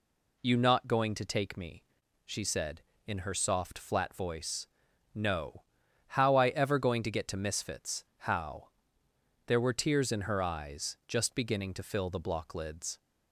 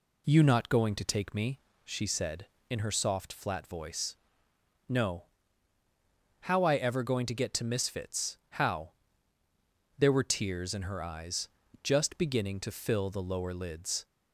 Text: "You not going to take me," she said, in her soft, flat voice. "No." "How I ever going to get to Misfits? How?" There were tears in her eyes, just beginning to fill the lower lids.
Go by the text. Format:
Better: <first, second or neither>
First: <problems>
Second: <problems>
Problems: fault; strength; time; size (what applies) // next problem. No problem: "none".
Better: second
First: says "block" for "lower"; at 12.2 s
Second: none